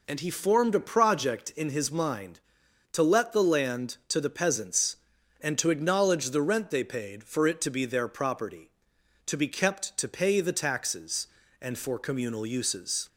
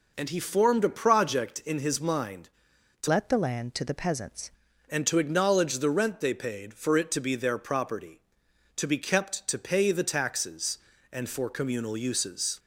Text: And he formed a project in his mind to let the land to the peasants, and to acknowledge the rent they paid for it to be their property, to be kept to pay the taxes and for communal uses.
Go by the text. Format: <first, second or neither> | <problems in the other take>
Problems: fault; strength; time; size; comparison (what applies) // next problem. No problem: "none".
first | changes voice from "let" to "peasants"; from 3.0 to 4.4 s; 1.4 s long